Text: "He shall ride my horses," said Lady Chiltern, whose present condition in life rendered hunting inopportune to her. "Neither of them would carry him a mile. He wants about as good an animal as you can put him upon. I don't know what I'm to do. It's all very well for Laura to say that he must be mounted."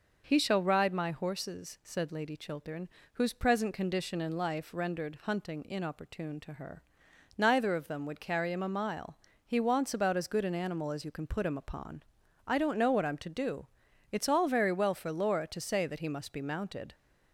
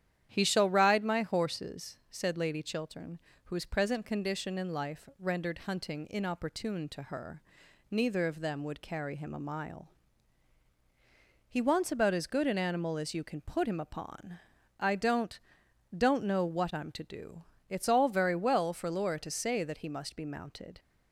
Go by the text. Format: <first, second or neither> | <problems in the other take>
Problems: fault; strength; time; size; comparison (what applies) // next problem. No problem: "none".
first | starts louder than the rest; strong; until 1.3 s; 10 dB // says "don't" twice; at 15.9 s